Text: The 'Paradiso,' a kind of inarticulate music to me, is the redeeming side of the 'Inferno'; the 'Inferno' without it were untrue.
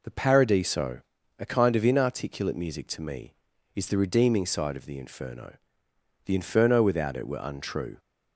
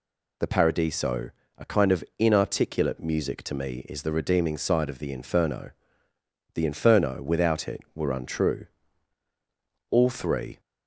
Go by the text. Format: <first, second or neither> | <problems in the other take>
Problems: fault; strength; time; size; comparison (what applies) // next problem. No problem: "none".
first | goes on to say "All three"; noticeable; from 9.8 s on; 0.70 s long